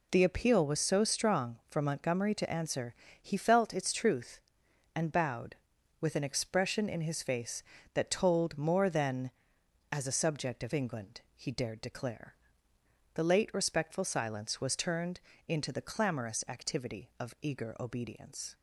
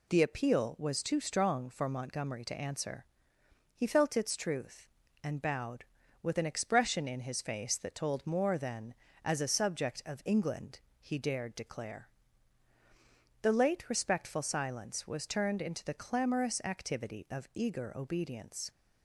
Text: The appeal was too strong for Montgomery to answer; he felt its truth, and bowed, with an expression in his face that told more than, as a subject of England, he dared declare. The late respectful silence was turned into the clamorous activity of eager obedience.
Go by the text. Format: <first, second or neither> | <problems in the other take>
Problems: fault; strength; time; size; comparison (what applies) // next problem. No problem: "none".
second | says "so" for "too"; at 0.7 s // pauses between "turned" and "into"; slight; at 15.2 s; 0.26 s long